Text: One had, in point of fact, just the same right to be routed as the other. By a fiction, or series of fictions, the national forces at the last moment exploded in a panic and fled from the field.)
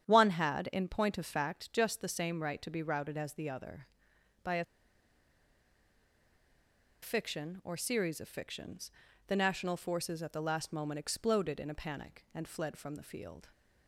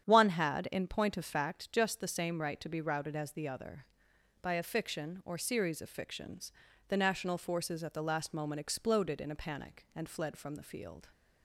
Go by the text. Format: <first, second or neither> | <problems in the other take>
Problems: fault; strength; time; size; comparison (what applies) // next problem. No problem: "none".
second | starts louder than the rest; strong; until 1.1 s; 8.5 dB; strong in the second // pauses between "a" and "fiction"; strong; at 4.6 s; 2.3 s long